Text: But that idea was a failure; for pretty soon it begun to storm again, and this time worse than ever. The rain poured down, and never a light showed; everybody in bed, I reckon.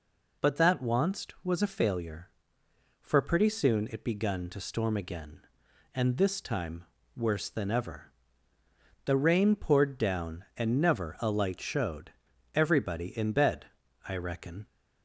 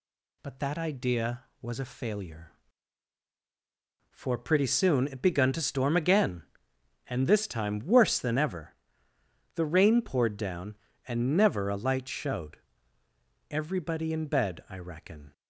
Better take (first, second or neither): second